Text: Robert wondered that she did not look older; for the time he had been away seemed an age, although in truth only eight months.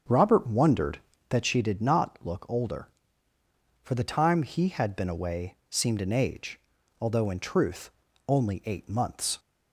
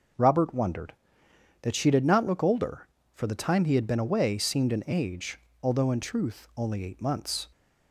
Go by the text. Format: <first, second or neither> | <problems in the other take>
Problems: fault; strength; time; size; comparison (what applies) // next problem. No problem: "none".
second | starts louder than the rest; until 1.3 s; 7 dB // pauses between "truth" and "only"; at 7.9 s; 0.38 s long